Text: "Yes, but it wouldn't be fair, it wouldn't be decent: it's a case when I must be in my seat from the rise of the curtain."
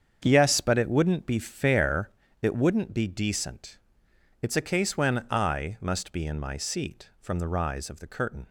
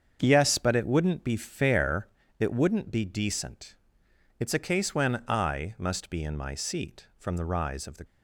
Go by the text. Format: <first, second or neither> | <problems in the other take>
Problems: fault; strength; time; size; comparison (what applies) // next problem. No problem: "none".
first | starts louder than the rest; strong; until 1.2 s; 7 dB; strong in the first // stops before "curtain"; at 8.0 s